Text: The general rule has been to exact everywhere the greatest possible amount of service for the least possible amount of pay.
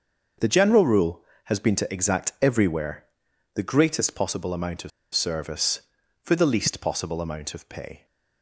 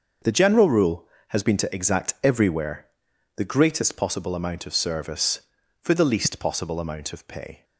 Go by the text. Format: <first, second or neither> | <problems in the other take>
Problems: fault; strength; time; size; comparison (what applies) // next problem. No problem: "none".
second | starts louder than the rest; until 1.6 s; 6.5 dB; also in the second // pauses between "everywhere" and "the"; noticeable; at 3.0 s; 0.50 s long; noticeable in the second // pauses between "of" and "service"; slight; at 4.9 s; 0.24 s long